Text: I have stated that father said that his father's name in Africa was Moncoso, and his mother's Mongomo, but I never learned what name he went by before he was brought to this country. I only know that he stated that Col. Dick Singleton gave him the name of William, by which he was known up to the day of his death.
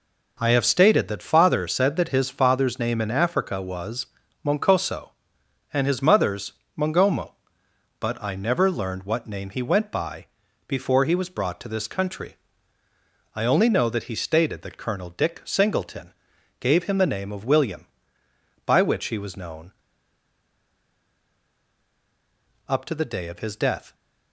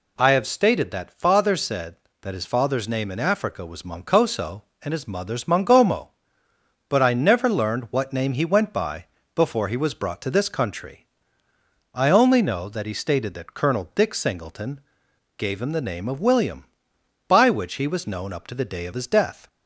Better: second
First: pauses between "was" and "Moncoso"; at 4.0 s; 0.38 s long // pauses between "mother's" and "Mongomo"; slight; at 6.5 s; 0.24 s long // pauses between "by" and "before"; at 10.2 s; 0.42 s long // pauses between "Singleton" and "gave"; noticeable; at 16.1 s; 0.48 s long // pauses between "known" and "up"; strong; at 19.7 s; 2.9 s long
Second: pauses between "by" and "before"; slight; at 9.0 s; 0.28 s long // pauses between "Singleton" and "gave"; noticeable; at 14.8 s; 0.58 s long

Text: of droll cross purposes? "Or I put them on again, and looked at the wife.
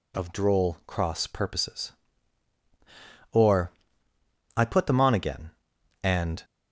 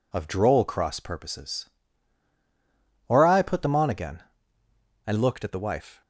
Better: second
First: pauses between "Or" and "I"; noticeable; at 3.7 s; 0.86 s long // stops before "looked at the wife"; at 6.4 s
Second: none

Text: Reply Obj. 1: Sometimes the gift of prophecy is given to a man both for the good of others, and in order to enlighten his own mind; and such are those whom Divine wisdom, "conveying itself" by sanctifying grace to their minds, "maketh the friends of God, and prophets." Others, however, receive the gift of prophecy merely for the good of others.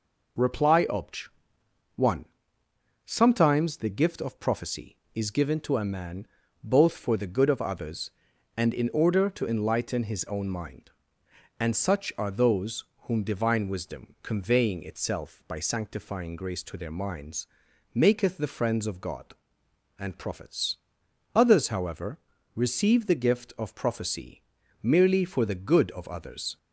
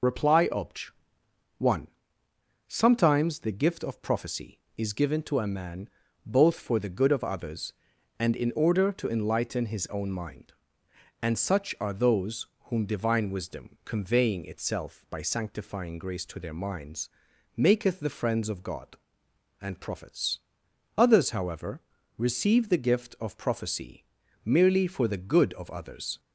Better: first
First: pauses between "man" and "both"; slight; at 6.2 s; 0.36 s long // pauses between "those" and "whom"; slight; at 12.8 s; 0.22 s long // pauses between "prophecy" and "merely"; at 24.4 s; 0.40 s long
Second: loses the start of "Reply"; at 0.0 s; 45 ms // pauses between "man" and "both"; slight; at 5.8 s; 0.36 s long // pauses between "those" and "whom"; slight; at 12.4 s; 0.22 s long // pauses between "prophecy" and "merely"; at 24.0 s; 0.40 s long

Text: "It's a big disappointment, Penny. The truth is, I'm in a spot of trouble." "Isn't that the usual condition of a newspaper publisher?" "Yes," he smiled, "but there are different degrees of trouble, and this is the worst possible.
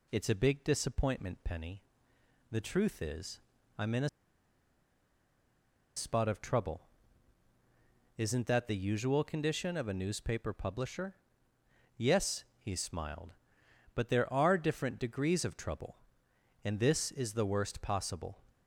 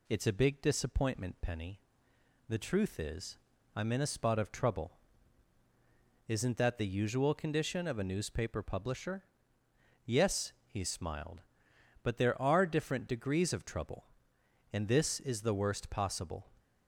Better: second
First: pauses between "a" and "spot"; strong; at 4.0 s; 1.8 s long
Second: none

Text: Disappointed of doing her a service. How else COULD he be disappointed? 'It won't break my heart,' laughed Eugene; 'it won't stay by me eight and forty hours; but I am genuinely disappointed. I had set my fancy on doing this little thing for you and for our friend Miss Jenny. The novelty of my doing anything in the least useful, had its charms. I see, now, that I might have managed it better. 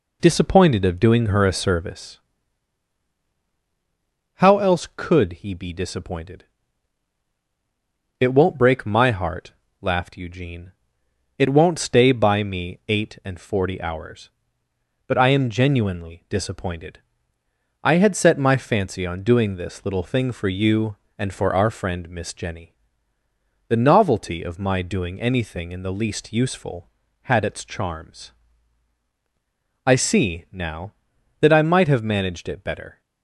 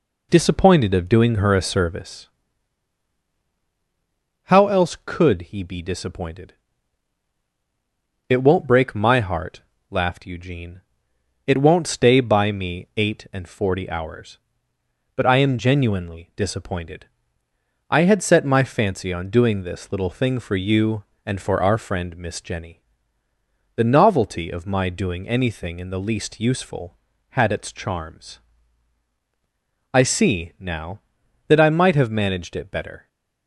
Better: neither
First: none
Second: none

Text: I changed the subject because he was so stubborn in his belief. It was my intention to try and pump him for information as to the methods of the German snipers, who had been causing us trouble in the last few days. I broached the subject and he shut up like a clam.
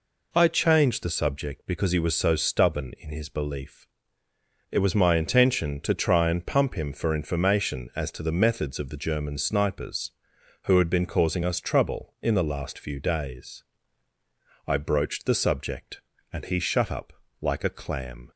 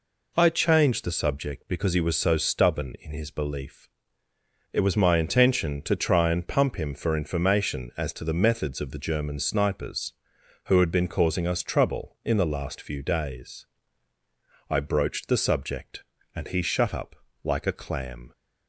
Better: neither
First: pauses between "up" and "like"; slight; at 17.1 s; 0.28 s long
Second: pauses between "up" and "like"; slight; at 17.1 s; 0.28 s long

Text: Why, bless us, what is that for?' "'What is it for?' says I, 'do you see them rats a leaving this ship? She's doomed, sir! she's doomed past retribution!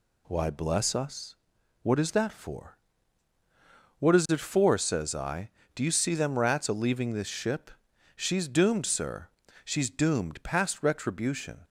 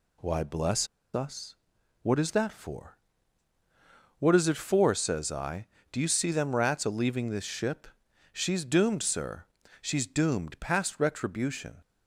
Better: first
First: none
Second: pauses between "bless" and "us"; slight; at 0.8 s; 0.28 s long

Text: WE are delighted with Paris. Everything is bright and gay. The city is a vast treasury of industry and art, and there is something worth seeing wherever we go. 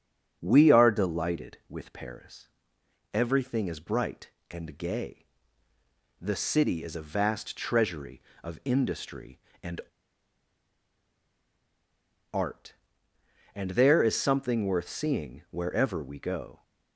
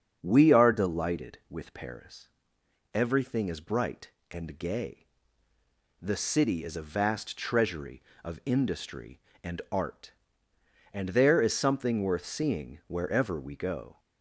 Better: second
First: starts louder than the rest; strong; until 1.4 s; 7 dB // pauses between "and" and "art"; strong; at 9.8 s; 2.5 s long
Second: starts louder than the rest; strong; until 1.2 s; 7 dB

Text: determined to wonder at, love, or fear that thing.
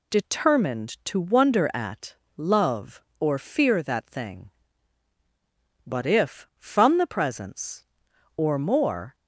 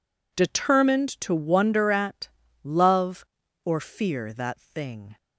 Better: second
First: goes on to say "But if from the presence or more"; strong; from 5.8 s on; 3.3 s long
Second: none

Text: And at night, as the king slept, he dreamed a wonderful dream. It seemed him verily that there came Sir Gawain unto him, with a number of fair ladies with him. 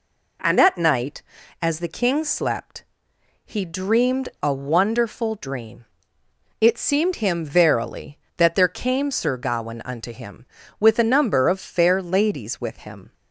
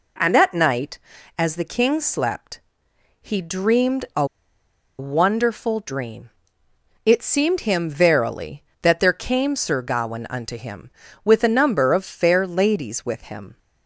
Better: first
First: none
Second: pauses between "a" and "wonderful"; noticeable; at 4.2 s; 0.73 s long

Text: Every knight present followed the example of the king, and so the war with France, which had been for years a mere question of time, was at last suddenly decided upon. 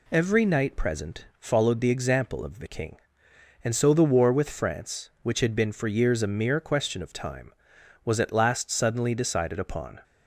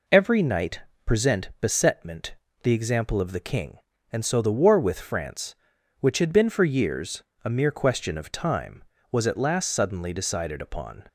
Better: first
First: none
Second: pauses between "knight" and "present"; slight; at 0.8 s; 0.22 s long // says "besetment" for "followed"; at 1.6 s // pauses between "years" and "a"; slight; at 7.2 s; 0.18 s long

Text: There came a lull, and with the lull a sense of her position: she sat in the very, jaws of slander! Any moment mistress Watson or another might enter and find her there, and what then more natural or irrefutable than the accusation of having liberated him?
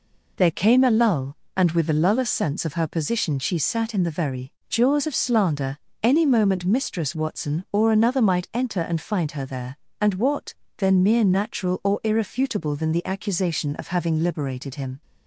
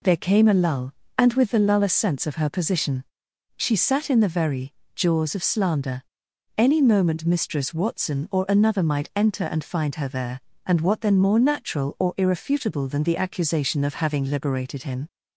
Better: second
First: pauses between "what" and "then"; slight; at 10.5 s; 0.22 s long // says "mere" for "more"; at 11.0 s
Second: none

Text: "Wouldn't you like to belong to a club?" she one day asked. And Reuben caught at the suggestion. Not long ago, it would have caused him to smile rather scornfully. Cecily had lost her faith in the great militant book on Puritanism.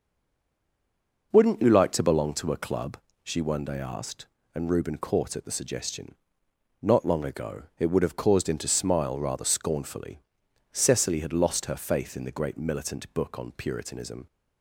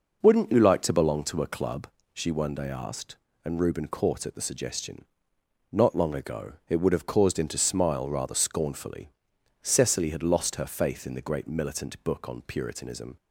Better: second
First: stays silent before the first word; noticeable; until 1.3 s; 1.3 s long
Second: none

